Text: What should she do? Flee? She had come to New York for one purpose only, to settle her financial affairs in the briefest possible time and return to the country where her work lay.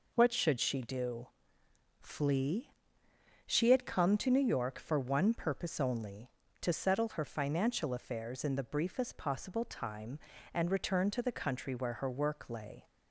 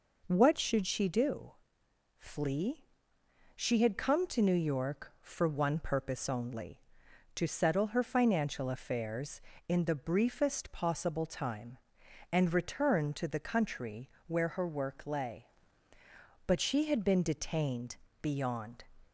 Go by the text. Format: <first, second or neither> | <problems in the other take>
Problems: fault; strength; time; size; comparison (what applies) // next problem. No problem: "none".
first | pauses between "country" and "where"; slight; at 14.0 s; 0.18 s long // goes on to say "But she had been detained beyond"; strong; from 16.4 s on; 2.3 s long